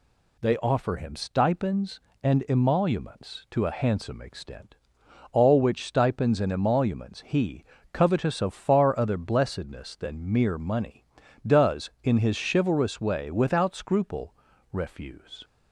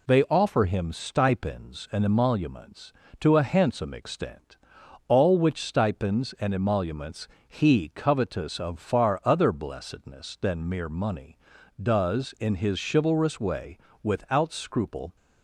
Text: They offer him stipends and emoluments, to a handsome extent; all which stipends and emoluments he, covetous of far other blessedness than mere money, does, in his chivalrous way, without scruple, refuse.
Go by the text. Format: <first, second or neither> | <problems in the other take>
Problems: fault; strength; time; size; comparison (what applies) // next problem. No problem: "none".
first | pauses between "emoluments" and "he"; slight; at 7.2 s; 0.20 s long // stops before "refuse"; at 15.1 s